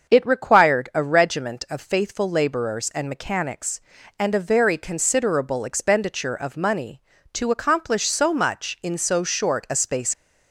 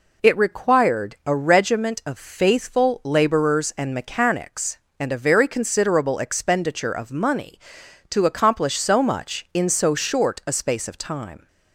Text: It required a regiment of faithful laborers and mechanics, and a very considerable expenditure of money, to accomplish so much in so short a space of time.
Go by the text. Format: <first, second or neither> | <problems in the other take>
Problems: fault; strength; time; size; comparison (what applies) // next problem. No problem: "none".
second | starts louder than the rest; until 1.1 s; 6.5 dB // stops before "of time"; at 10.1 s